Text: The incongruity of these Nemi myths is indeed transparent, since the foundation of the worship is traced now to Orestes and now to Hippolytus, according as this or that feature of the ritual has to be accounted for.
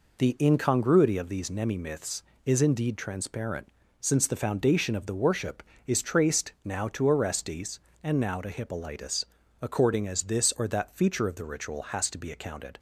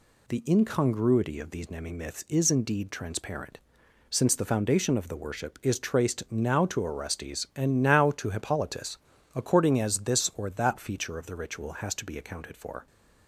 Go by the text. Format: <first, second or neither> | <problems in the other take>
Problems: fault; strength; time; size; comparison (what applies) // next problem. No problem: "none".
second | stops before "for"; at 12.7 s